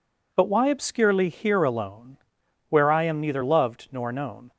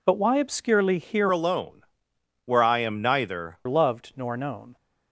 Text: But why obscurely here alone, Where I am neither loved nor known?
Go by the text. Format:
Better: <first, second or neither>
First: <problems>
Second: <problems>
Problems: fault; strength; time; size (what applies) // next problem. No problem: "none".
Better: first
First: none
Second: changes voice from "alone" to "neither"; from 1.3 to 3.5 s; 2.2 s long